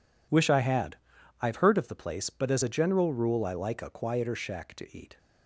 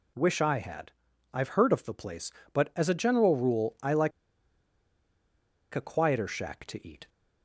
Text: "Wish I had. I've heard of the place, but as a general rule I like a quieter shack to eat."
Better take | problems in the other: first | pauses between "like" and "a"; strong; at 4.1 s; 1.6 s long

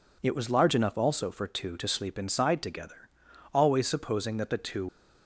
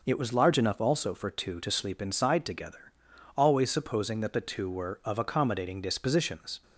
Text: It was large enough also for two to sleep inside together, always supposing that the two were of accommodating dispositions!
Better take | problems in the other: second | stops before "were of accommodating dispositions"; at 4.8 s

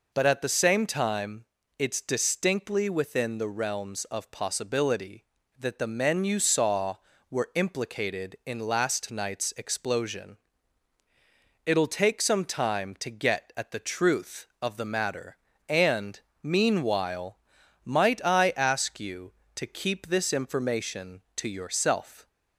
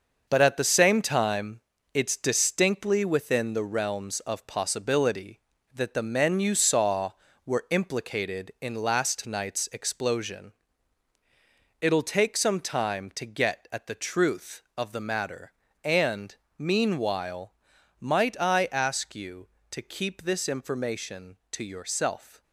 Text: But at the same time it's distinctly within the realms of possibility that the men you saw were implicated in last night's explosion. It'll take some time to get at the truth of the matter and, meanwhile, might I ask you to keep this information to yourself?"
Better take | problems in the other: first | gets quieter; strong; throughout; 7 dB // pauses between "time" and "it's"; slight; at 1.6 s; 0.34 s long; slight in the first

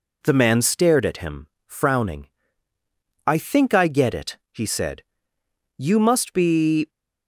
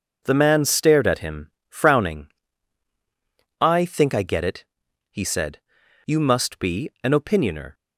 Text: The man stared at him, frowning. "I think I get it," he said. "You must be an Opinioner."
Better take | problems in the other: second | stops before "an Opinioner"; at 6.8 s

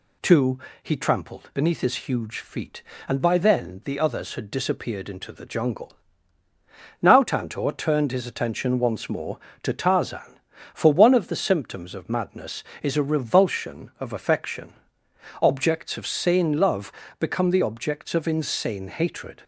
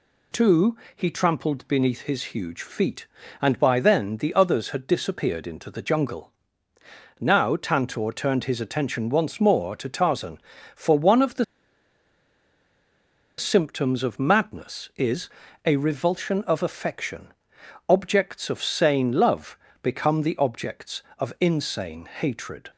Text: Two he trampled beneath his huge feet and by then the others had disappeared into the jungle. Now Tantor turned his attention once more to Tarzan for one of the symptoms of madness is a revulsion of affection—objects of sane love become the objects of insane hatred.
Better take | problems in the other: first | pauses between "Two" and "he"; slight; at 0.7 s; 0.20 s long; slight in the first // pauses between "the" and "symptoms"; strong; at 11.4 s; 1.9 s long // pauses between "is" and "a"; slight; at 15.2 s; 0.36 s long // pauses between "love" and "become"; slight; at 19.5 s; 0.26 s long; slight in the first

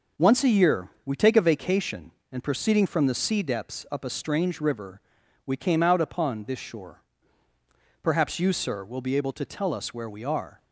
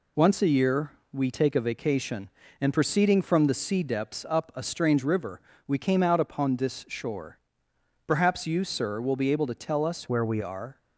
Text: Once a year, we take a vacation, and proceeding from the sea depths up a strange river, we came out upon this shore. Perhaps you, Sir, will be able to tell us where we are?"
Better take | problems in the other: first | changes voice from "where" to "we"; from 10.0 to 10.3 s; 0.3 s long

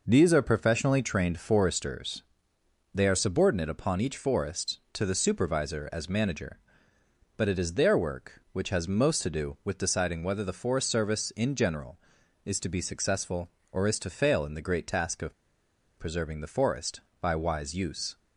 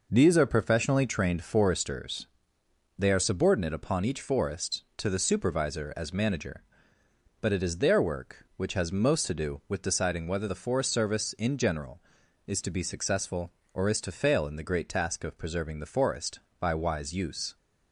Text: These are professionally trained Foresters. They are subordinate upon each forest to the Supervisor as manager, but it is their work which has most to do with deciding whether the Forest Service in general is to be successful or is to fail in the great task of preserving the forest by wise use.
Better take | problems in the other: second | pauses between "of" and "preserving"; noticeable; at 15.3 s; 0.64 s long

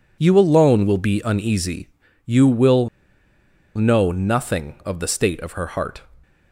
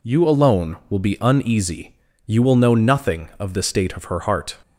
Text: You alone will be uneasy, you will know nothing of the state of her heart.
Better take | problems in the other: second | pauses between "will" and "know"; noticeable; at 2.8 s; 0.87 s long

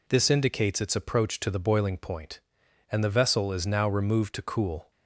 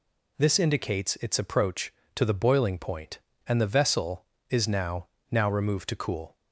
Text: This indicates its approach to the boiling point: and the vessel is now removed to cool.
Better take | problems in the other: first | says "now" twice; at 5.3 s

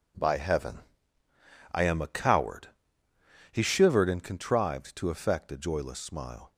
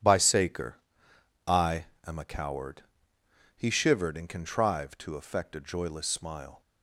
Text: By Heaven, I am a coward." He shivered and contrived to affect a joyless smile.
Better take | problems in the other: first | says "Saker" for "Heaven"; at 0.1 s // pauses between "I" and "am"; slight; at 1.8 s; 0.20 s long

